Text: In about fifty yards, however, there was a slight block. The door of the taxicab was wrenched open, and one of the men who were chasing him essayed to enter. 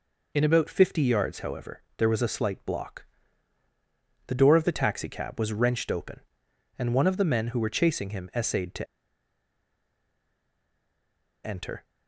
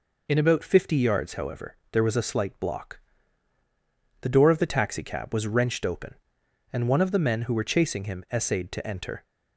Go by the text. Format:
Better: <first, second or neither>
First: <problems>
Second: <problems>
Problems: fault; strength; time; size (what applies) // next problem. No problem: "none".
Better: second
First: pauses between "to" and "enter"; strong; at 8.8 s; 2.5 s long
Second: none